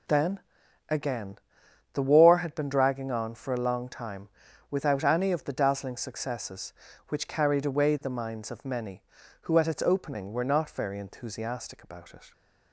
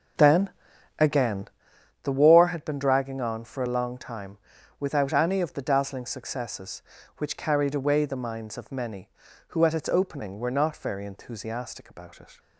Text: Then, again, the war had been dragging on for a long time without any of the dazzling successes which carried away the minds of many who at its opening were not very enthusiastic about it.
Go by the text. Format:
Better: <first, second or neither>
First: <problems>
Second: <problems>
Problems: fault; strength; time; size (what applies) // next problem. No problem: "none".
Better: first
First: pauses between "time" and "without"; at 4.2 s; 0.42 s long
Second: starts louder than the rest; noticeable; until 1.6 s; 5.5 dB // pauses between "time" and "without"; at 4.3 s; 0.42 s long